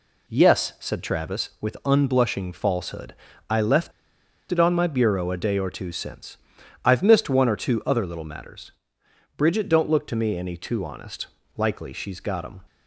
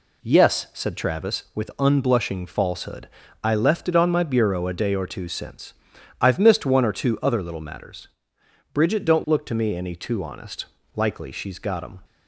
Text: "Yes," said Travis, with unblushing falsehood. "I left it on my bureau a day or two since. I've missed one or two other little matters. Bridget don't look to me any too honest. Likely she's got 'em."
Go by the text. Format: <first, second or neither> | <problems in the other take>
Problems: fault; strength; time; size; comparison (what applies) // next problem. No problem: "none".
second | pauses between "left" and "it"; noticeable; at 3.9 s; 0.60 s long